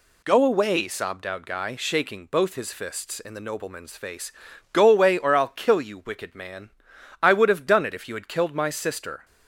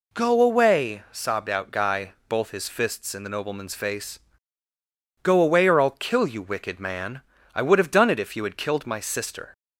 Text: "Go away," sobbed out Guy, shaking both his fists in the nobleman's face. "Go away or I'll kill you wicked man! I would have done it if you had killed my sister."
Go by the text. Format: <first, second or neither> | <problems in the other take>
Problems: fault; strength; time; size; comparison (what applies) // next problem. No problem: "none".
first | skips "shaking"; at 2.1 s